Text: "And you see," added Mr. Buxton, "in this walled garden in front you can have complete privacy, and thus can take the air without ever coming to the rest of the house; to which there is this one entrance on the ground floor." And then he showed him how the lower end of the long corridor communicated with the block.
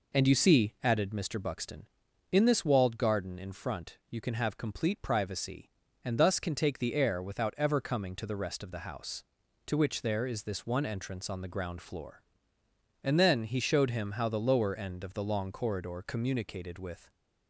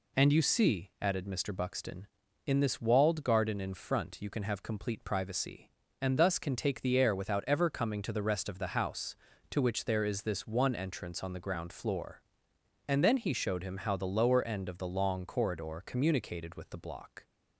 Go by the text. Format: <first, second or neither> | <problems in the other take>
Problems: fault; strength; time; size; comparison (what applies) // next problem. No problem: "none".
second | stops before "the block"; at 17.0 s